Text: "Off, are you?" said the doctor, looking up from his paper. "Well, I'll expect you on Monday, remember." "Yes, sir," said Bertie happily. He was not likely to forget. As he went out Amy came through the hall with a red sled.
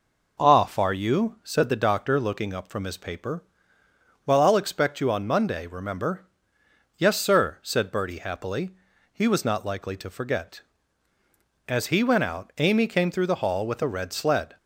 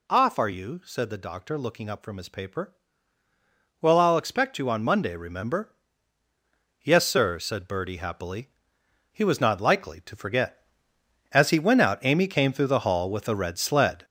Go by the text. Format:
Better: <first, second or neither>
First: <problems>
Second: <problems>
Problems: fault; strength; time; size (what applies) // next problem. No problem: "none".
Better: first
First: none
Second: gets louder; throughout; 6.5 dB